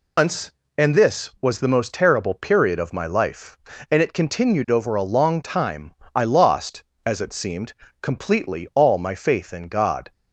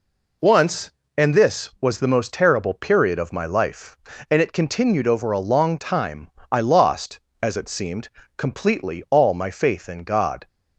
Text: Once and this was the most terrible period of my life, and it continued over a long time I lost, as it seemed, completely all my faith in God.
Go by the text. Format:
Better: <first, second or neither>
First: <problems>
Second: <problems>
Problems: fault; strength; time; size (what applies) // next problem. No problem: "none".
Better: second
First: loses the start of "Once"; at 0.1 s; 155 ms // pauses between "time" and "I"; slight; at 5.9 s; 0.20 s long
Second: pauses between "time" and "I"; slight; at 6.2 s; 0.20 s long